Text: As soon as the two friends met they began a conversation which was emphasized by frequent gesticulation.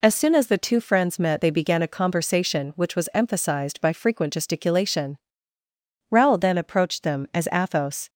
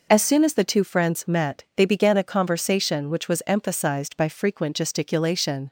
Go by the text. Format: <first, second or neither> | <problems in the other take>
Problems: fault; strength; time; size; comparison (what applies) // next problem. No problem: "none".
second | goes on to say "Raoul then approached them as Athos"; strong; from 6.1 s on; 1.9 s long